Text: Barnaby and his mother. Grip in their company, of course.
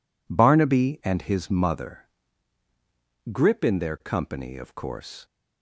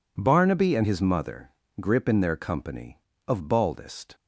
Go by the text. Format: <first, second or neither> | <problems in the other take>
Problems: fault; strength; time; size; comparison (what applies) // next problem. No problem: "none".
first | says "baldest" for "course"; at 3.4 s